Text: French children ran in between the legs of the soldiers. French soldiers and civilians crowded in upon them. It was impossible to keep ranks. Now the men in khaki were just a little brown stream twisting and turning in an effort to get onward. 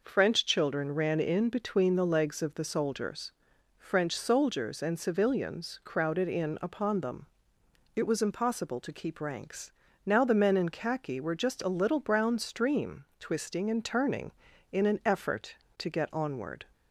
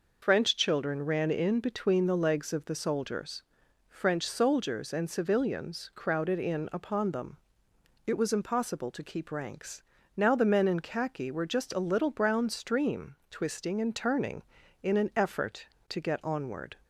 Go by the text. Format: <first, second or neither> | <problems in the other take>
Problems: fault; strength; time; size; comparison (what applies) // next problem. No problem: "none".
first | loses the start of "French"; at 0.2 s; 80 ms